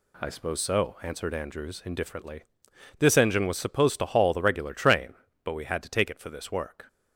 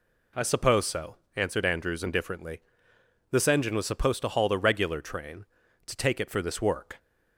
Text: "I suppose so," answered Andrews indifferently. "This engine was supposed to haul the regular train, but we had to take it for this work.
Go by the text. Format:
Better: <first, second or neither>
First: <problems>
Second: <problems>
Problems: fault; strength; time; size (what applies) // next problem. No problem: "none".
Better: first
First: none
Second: skips "but we had"; at 5.6 s